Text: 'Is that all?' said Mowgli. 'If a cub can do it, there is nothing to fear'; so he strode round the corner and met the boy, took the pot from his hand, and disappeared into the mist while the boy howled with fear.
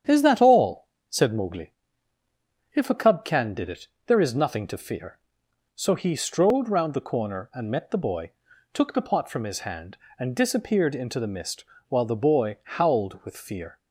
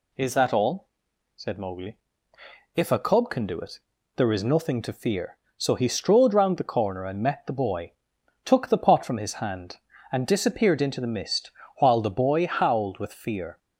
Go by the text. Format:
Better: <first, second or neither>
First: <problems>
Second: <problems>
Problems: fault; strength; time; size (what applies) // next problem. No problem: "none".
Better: second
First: starts louder than the rest; strong; until 1.3 s; 9 dB // says "did" for "do"; at 3.5 s // pauses between "mist" and "while"; slight; at 11.6 s; 0.24 s long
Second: pauses between "mist" and "while"; slight; at 11.5 s; 0.28 s long